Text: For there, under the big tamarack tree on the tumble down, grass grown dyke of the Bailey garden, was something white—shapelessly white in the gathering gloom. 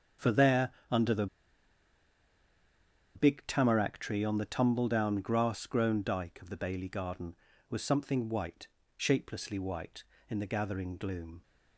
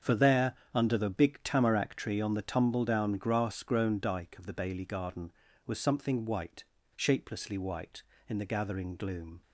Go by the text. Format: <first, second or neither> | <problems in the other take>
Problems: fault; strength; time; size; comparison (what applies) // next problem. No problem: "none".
second | starts louder than the rest; strong; until 3.3 s; 7.5 dB; strong in the second // pauses between "the" and "big"; strong; at 1.2 s; 1.8 s long